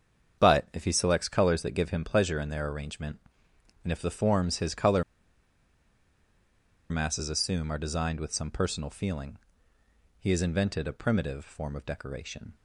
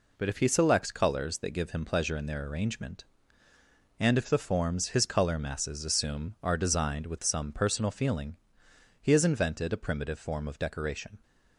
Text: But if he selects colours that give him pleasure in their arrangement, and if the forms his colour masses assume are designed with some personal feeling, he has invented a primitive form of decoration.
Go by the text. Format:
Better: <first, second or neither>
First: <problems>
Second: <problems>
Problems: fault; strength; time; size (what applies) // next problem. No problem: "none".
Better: second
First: starts louder than the rest; strong; until 1.4 s; 7.5 dB // pauses between "colour" and "masses"; strong; at 5.0 s; 1.8 s long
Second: none